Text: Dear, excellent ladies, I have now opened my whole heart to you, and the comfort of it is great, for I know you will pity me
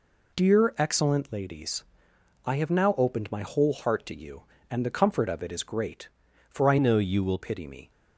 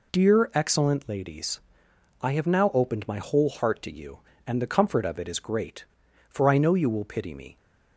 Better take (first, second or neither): second